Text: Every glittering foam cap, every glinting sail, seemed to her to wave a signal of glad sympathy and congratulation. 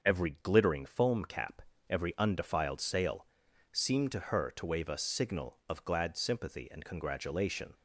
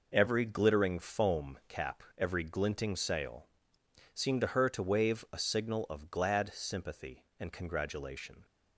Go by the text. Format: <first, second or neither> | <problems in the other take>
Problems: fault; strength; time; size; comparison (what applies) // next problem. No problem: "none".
second | starts louder than the rest; until 1.0 s; 6.5 dB // says "undefiled" for "glinting"; at 2.1 s